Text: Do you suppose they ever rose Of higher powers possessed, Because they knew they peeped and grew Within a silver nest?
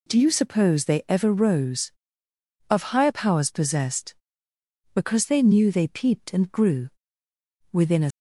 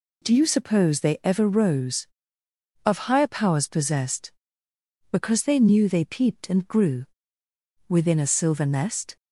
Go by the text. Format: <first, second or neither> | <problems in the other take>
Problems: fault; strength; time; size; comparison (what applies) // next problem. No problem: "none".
second | pauses between "grew" and "Within"; noticeable; at 6.8 s; 0.82 s long; noticeable in the second // stops before "silver nest"; at 8.1 s